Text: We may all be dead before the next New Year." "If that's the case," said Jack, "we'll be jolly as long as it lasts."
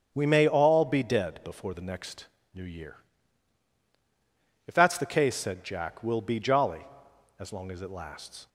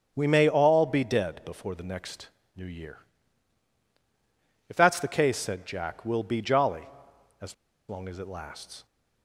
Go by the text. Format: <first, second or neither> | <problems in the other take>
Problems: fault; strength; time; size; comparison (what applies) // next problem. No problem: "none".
first | starts louder than the rest; strong; until 1.1 s; 7.5 dB; strong in the first // pauses between "next" and "New"; slight; at 2.2 s; 0.28 s long; slight in the first // pauses between "as" and "long"; slight; at 7.5 s; 0.34 s long